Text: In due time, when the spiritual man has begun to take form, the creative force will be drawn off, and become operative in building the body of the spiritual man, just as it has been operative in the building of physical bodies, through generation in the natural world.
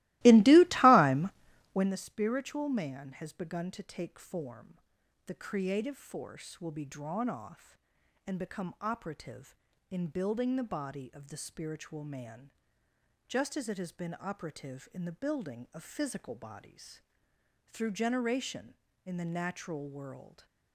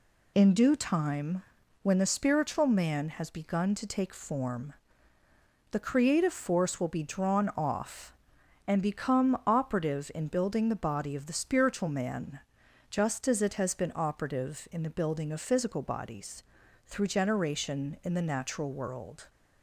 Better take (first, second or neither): second